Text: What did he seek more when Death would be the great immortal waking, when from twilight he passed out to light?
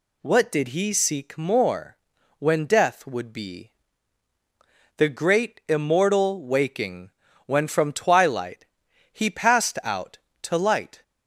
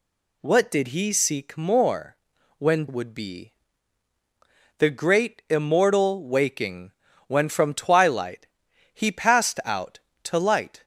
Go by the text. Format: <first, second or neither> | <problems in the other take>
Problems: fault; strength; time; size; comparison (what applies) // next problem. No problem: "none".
first | pauses between "more" and "when"; at 2.1 s; 0.44 s long; also in the first // skips "Death"; at 2.8 s // pauses between "be" and "the"; strong; at 3.5 s; 1.2 s long; strong in the first // pauses between "twilight" and "he"; noticeable; at 8.4 s; 0.48 s long; noticeable in the first